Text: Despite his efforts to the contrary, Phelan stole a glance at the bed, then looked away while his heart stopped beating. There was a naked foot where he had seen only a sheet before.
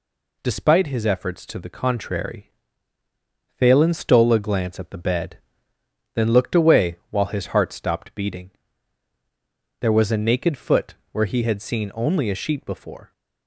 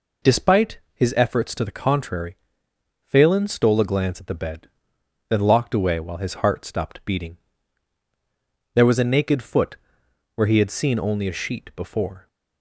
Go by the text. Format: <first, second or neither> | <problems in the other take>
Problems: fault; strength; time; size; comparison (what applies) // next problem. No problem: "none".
first | pauses between "Despite" and "his"; slight; at 0.7 s; 0.16 s long // says "locked" for "looked"; at 5.3 s // pauses between "foot" and "where"; noticeable; at 9.7 s; 0.58 s long; slight in the first